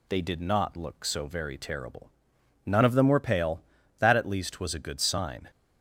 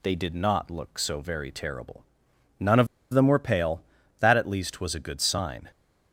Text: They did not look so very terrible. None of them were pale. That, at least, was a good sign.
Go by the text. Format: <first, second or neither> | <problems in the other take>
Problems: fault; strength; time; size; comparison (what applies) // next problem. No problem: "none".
first | pauses between "of" and "them"; slight; at 2.8 s; 0.25 s long